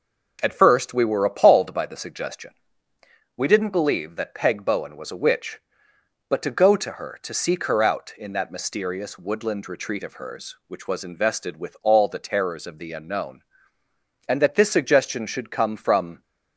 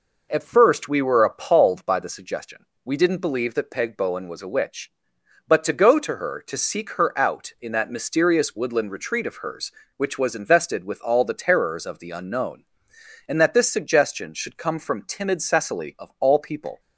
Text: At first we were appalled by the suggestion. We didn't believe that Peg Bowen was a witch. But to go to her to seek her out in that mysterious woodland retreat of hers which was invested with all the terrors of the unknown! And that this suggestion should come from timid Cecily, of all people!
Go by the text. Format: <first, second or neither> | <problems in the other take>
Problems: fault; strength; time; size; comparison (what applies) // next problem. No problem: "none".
second | stops before "timid Cecily of all people"; at 16.2 s